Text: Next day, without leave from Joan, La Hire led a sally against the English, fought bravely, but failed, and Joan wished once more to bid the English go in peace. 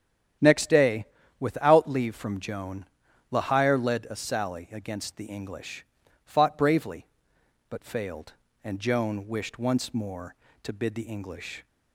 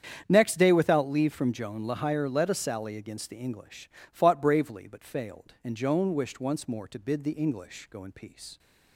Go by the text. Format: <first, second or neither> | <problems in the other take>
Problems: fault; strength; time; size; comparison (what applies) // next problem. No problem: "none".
second | starts louder than the rest; strong; until 1.7 s; 9.5 dB; strong in the second // stops before "go in peace"; at 11.6 s